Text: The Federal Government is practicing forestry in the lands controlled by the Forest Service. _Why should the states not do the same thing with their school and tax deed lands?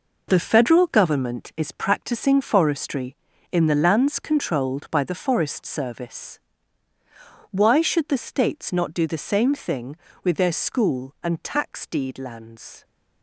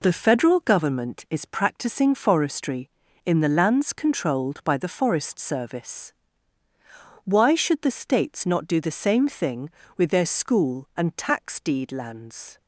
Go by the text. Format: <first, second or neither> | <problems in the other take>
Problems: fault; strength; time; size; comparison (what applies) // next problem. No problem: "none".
second | gets quieter; strong; throughout; 8.5 dB